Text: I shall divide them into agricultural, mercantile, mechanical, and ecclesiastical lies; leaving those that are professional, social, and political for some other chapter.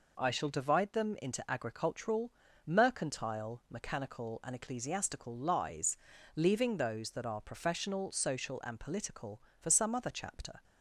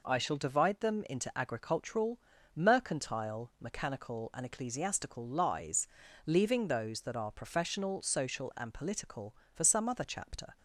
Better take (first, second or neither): neither